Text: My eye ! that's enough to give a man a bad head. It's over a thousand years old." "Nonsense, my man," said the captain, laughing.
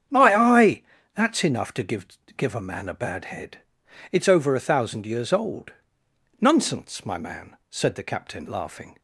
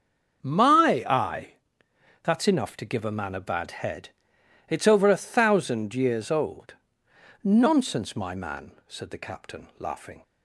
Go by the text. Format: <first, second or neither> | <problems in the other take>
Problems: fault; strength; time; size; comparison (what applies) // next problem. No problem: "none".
second | starts louder than the rest; strong; until 1.4 s; 8.5 dB; also in the second // says "give" twice; at 2.3 s